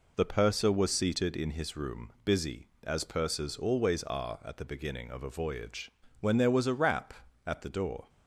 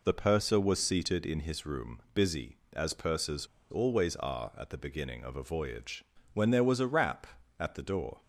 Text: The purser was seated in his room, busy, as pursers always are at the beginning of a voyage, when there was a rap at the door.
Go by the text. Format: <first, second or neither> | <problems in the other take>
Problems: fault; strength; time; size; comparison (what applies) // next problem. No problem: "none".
first | pauses between "pursers" and "always"; slight; at 3.4 s; 0.23 s long